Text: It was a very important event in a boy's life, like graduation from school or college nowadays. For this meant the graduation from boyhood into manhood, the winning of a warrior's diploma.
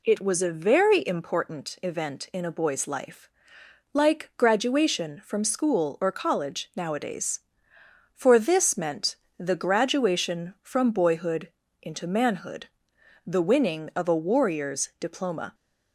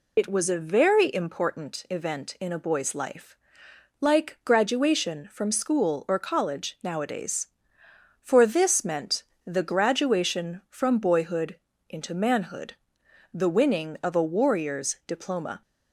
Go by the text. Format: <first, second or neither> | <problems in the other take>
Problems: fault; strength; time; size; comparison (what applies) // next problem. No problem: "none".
first | loses the start of "It"; at 0.1 s; 60 ms // pauses between "meant" and "the"; slight; at 9.2 s; 0.22 s long; slight in the first // pauses between "boyhood" and "into"; slight; at 11.5 s; 0.32 s long; slight in the first